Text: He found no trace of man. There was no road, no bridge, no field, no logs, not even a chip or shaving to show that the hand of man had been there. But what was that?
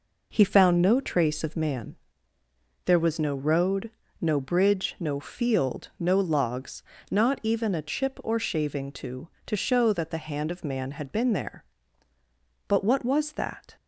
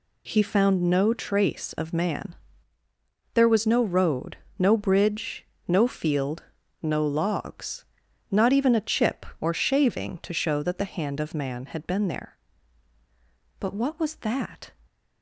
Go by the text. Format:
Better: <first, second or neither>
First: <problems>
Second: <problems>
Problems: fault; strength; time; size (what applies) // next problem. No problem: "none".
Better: second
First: says "to" twice; at 9.4 s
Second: none